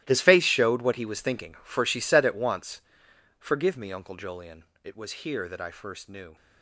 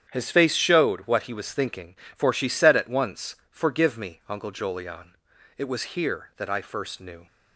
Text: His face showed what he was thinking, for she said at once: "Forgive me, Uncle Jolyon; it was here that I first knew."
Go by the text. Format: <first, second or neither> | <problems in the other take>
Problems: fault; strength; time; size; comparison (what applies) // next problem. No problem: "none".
second | gets quieter; strong; throughout; 16.5 dB // starts louder than the rest; strong; until 1.0 s; 16 dB; strong in the second